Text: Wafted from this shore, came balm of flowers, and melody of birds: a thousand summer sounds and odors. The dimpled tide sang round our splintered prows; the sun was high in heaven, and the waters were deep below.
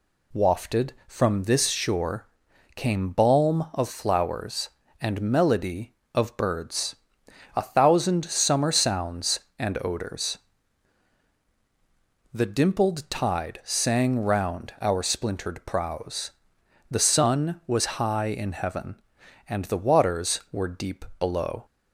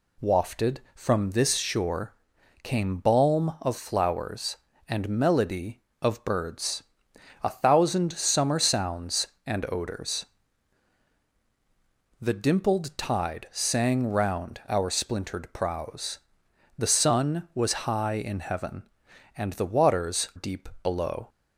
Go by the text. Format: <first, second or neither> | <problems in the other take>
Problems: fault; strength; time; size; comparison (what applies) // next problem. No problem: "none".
first | skips "were"; at 20.3 s // pauses between "deep" and "below"; slight; at 20.6 s; 0.16 s long; slight in the first